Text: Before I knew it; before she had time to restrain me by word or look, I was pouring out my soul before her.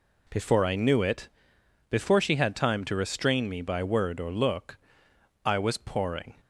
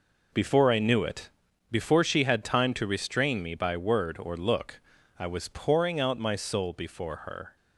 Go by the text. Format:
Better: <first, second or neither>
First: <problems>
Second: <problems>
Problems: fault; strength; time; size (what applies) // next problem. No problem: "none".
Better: second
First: stops before "out my soul before her"; at 6.4 s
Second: none